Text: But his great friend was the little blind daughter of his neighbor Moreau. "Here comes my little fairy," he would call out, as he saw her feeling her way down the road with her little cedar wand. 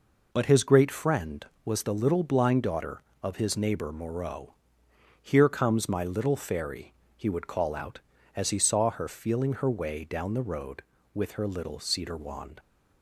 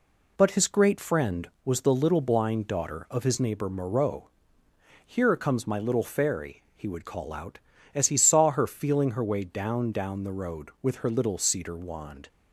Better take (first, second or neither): first